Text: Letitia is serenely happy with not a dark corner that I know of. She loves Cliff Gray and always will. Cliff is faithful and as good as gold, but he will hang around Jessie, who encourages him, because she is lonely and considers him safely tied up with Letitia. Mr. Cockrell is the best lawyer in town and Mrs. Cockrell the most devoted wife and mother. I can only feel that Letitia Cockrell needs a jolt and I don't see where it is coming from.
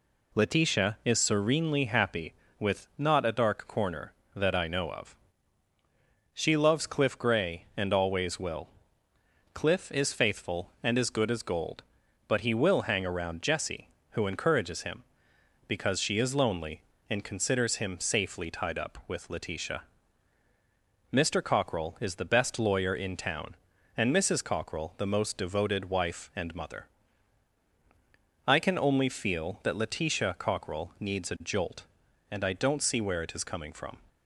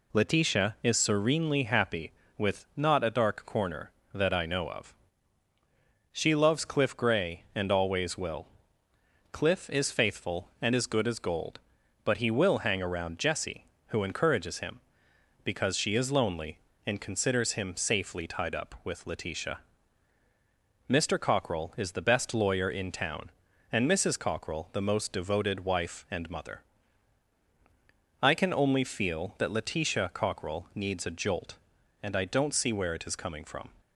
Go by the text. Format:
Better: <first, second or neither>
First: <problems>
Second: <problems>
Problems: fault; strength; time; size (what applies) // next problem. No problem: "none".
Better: neither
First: none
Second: none